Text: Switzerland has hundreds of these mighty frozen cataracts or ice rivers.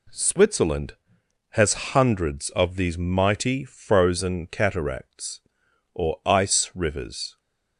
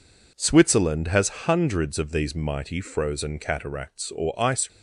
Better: first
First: none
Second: stops before "rivers"; at 4.6 s

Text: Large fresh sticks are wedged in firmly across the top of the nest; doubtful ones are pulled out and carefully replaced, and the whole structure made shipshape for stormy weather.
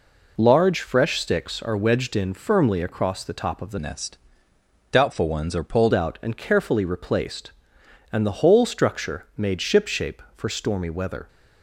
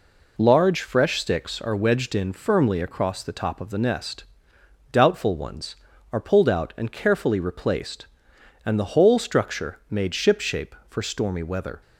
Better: second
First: changes voice from "nest" to "pulled"; from 3.7 to 5.9 s; 2.2 s long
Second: none

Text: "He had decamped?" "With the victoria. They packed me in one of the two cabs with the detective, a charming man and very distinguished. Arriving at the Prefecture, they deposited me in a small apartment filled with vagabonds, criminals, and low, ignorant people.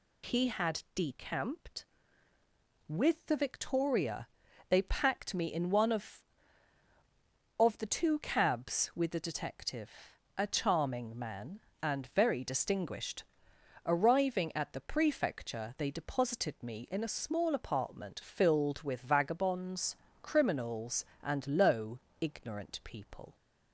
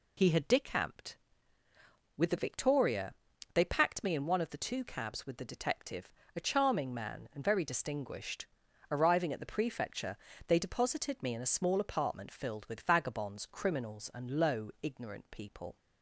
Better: second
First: says "of" twice; at 7.5 s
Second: none

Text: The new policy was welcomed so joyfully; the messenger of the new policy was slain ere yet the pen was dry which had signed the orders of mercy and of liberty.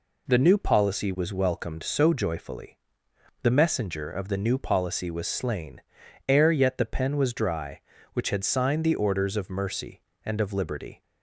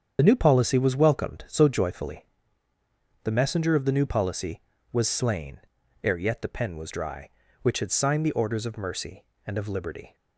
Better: first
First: pauses between "slain" and "ere"; noticeable; at 5.7 s; 0.48 s long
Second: loses the start of "The"; at 0.1 s; 40 ms // starts louder than the rest; strong; until 1.2 s; 7.5 dB // pauses between "slain" and "ere"; at 5.5 s; 0.44 s long

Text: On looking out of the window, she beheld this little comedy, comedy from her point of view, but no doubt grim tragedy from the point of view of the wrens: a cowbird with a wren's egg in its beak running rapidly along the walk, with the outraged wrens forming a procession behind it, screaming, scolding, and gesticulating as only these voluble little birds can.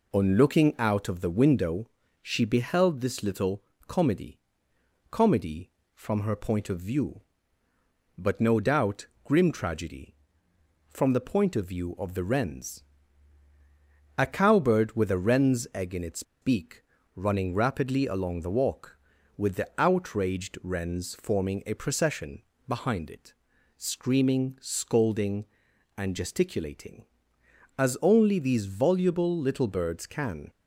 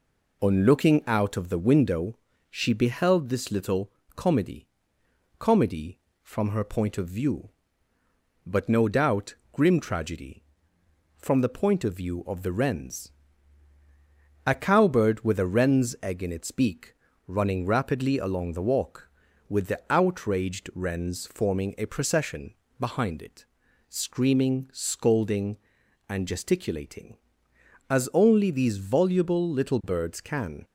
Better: second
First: pauses between "little" and "comedy"; slight; at 3.6 s; 0.26 s long // pauses between "doubt" and "grim"; slight; at 9.0 s; 0.18 s long // pauses between "its" and "beak"; slight; at 16.2 s; 0.19 s long // pauses between "beak" and "running"; slight; at 16.8 s; 0.34 s long // pauses between "procession" and "behind"; slight; at 22.4 s; 0.26 s long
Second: pauses between "little" and "comedy"; slight; at 3.9 s; 0.26 s long // pauses between "doubt" and "grim"; slight; at 9.3 s; 0.18 s long // pauses between "beak" and "running"; slight; at 16.9 s; 0.34 s long // pauses between "procession" and "behind"; slight; at 22.5 s; 0.26 s long

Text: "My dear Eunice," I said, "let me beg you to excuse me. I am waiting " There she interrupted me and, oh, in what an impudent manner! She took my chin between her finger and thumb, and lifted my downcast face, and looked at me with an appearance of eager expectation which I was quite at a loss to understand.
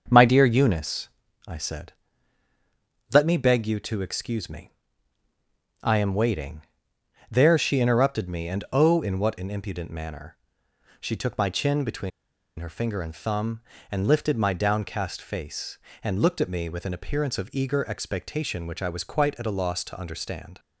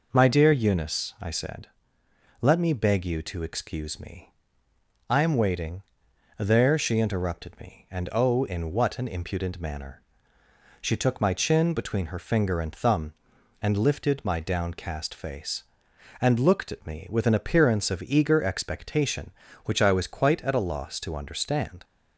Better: second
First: starts louder than the rest; until 1.0 s; 6.5 dB // pauses between "between" and "her"; noticeable; at 12.1 s; 0.48 s long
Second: none

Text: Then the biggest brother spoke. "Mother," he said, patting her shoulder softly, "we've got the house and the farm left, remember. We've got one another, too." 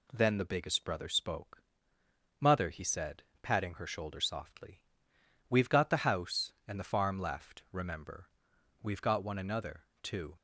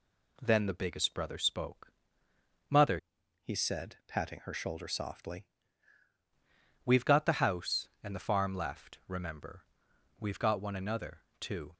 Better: first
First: none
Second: changes voice from "he" to "softly"; from 3.4 to 5.4 s; 2.0 s long

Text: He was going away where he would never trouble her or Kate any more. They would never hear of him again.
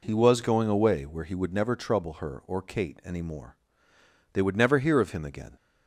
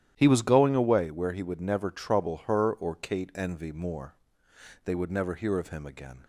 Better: first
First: none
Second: starts louder than the rest; strong; until 1.1 s; 11.5 dB // says "envy" for "any"; at 3.3 s

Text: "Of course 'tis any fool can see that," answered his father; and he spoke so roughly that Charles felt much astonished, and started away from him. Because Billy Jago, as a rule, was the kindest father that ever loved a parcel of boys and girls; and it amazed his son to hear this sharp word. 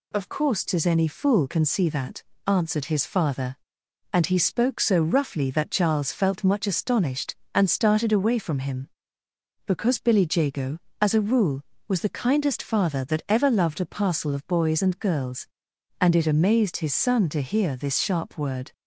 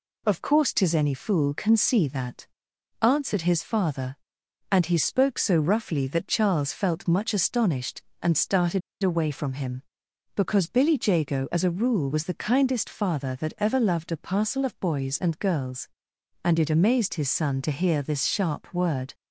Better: first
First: none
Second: pauses between "started" and "away"; slight; at 8.8 s; 0.23 s long

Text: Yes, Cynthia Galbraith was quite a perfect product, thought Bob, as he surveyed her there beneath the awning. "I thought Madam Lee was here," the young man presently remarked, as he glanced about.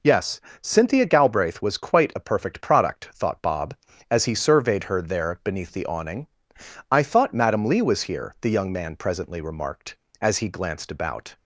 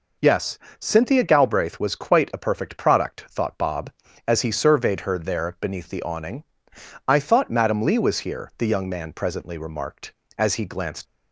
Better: first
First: none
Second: stops before "about"; at 11.0 s

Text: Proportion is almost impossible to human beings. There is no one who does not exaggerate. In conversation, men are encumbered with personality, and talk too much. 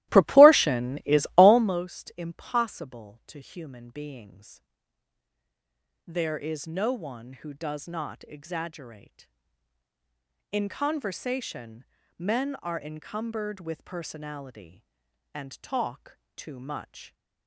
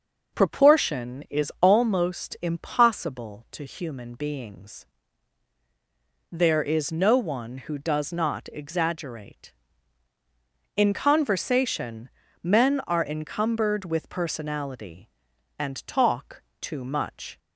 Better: second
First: starts louder than the rest; strong; until 1.8 s; 16 dB // pauses between "talk" and "too"; slight; at 16.1 s; 0.18 s long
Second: pauses between "talk" and "too"; slight; at 16.4 s; 0.18 s long

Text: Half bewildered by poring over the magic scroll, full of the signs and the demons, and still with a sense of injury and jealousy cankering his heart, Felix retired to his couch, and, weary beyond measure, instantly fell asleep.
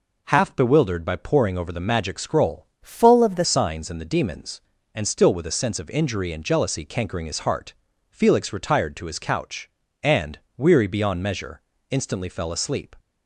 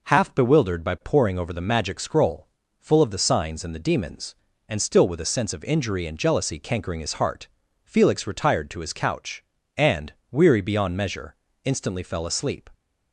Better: second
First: changes voice from "full" to "the"; from 2.8 to 3.4 s; 0.6 s long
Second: none

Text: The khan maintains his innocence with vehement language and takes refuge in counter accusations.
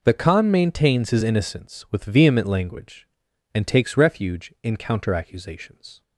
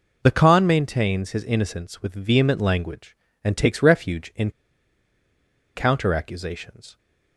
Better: first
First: none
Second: pauses between "in" and "counter"; strong; at 4.4 s; 1.2 s long

